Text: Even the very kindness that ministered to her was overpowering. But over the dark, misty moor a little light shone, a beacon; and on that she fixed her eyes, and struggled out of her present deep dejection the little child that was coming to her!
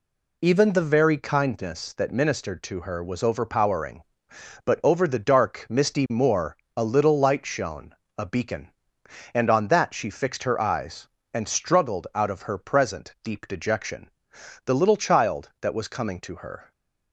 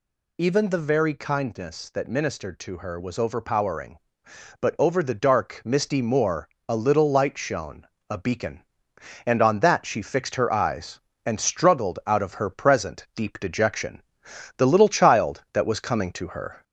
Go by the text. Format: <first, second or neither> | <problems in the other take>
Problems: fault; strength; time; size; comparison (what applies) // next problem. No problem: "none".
first | gets louder; slight; throughout; 2.5 dB // pauses between "moor" and "a"; slight; at 6.4 s; 0.18 s long; slight in the first // pauses between "dejection" and "the"; noticeable; at 14.0 s; 0.56 s long; noticeable in the first